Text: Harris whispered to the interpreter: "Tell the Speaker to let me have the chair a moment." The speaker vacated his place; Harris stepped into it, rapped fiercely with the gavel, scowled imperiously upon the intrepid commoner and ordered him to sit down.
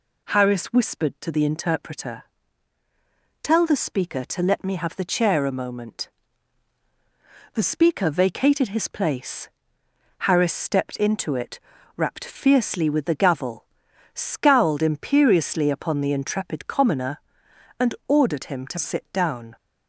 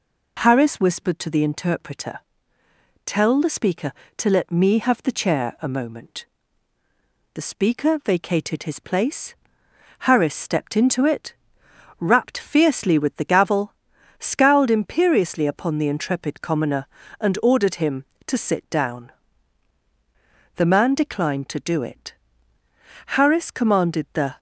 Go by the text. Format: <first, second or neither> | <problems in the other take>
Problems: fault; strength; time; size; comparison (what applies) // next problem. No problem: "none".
first | goes on to say "The man declined to do it Harris commanded the"; strong; from 20.5 s on; 3.8 s long